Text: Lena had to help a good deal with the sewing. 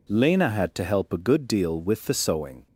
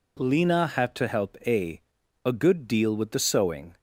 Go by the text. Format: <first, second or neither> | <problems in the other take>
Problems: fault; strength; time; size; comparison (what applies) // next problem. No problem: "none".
first | says "a" twice; at 2.2 s